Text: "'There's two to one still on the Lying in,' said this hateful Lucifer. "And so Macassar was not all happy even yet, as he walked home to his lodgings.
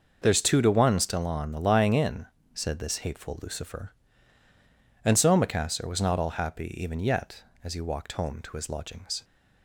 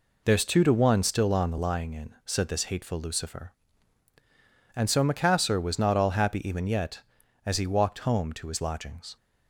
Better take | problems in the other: neither | none

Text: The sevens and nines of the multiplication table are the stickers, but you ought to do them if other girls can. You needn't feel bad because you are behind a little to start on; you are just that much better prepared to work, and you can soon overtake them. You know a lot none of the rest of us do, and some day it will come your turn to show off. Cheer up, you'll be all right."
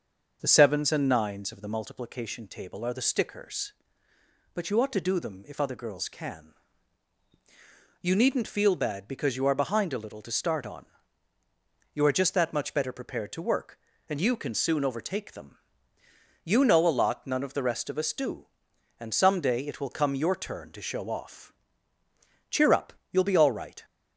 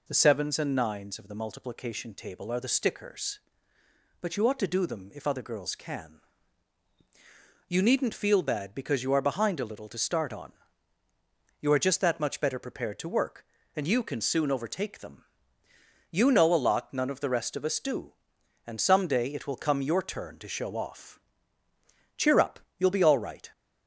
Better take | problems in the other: second | starts louder than the rest; until 1.9 s; 6.5 dB

